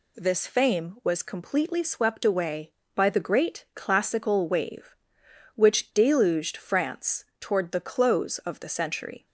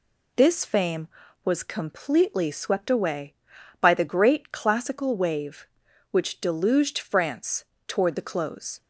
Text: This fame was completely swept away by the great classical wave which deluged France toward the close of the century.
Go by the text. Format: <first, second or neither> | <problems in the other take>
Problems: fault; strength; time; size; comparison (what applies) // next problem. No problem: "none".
first | pauses between "France" and "toward"; slight; at 7.6 s; 0.24 s long; slight in the first // stops before "of the century"; at 8.8 s